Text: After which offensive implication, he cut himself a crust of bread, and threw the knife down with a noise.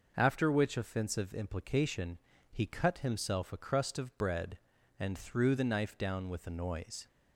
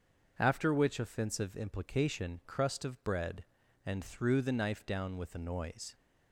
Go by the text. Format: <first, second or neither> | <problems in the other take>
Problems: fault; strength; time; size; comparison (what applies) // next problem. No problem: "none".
first | starts louder than the rest; until 1.3 s; 6.5 dB // skips "he cut himself a"; at 2.4 s